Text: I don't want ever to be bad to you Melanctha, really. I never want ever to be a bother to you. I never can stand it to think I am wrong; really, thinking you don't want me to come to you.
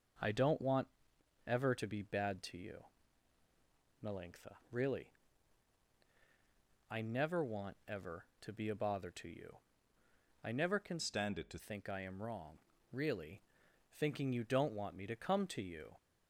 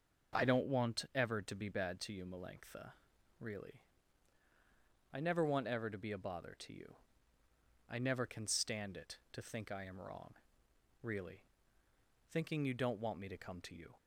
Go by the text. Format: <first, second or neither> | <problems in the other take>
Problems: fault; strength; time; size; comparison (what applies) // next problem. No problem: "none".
second | pauses between "want" and "ever"; noticeable; at 0.8 s; 0.58 s long // pauses between "you" and "Melanctha"; strong; at 2.7 s; 1.2 s long // changes voice from "stand" to "to"; from 10.9 to 11.5 s; 0.6 s long